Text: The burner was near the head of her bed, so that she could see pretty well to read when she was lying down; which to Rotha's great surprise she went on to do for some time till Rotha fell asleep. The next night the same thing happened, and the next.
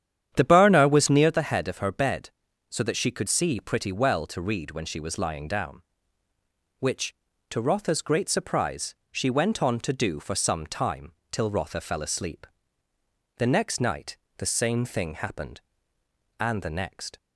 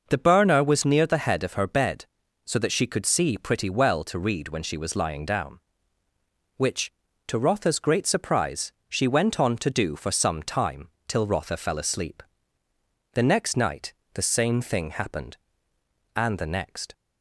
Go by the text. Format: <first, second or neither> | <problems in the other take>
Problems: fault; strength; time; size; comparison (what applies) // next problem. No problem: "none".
second | starts louder than the rest; strong; until 1.4 s; 9.5 dB // pauses between "surprise" and "she"; slight; at 8.9 s; 0.16 s long; slight in the second // pauses between "time" and "till"; slight; at 11.1 s; 0.18 s long; slight in the second // pauses between "night" and "the"; slight; at 14.1 s; 0.18 s long; slight in the second